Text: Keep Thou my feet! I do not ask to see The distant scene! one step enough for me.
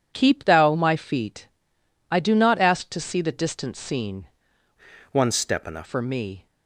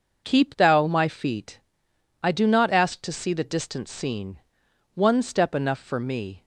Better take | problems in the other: second | changes voice from "one" to "enough"; from 5.1 to 5.8 s; 0.7 s long

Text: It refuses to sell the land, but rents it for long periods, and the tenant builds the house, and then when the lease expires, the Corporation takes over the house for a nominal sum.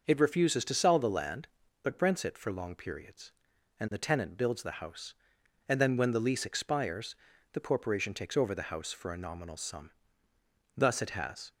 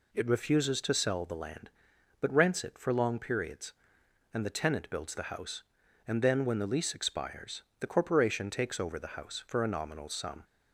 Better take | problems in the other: second | starts louder than the rest; until 1.0 s; 6 dB // goes on to say "Thus it has"; noticeable; from 10.7 s on; 0.76 s long

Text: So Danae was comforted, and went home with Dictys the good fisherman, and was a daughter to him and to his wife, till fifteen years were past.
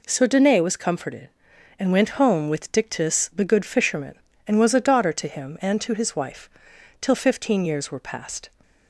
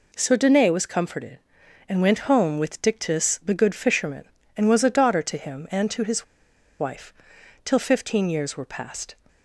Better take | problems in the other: first | pauses between "his" and "wife"; noticeable; at 6.2 s; 0.55 s long

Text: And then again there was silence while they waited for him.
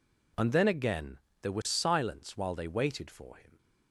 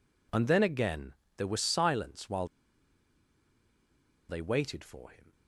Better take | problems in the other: first | pauses between "again" and "there"; slight; at 1.1 s; 0.24 s long; slight in the first // pauses between "while" and "they"; strong; at 2.4 s; 1.8 s long

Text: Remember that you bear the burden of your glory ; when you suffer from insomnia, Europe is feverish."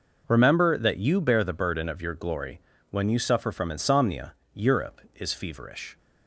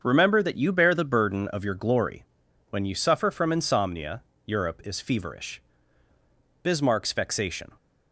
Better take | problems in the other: first | starts louder than the rest; until 1.0 s; 7 dB // goes on to say "Bismarck's vexation"; noticeable; from 6.6 s on; 1.0 s long

